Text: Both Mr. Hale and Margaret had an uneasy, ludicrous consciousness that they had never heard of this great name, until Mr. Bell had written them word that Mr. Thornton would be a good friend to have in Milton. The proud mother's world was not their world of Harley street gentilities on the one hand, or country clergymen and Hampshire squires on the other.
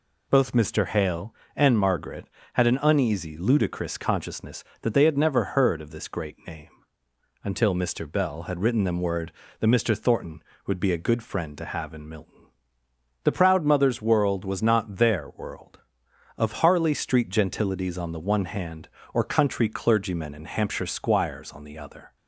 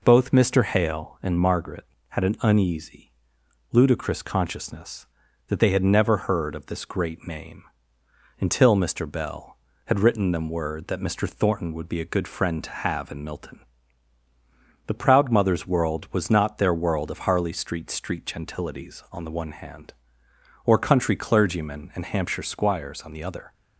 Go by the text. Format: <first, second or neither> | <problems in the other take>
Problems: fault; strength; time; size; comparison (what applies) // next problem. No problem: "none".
first | says "street" twice; at 17.8 s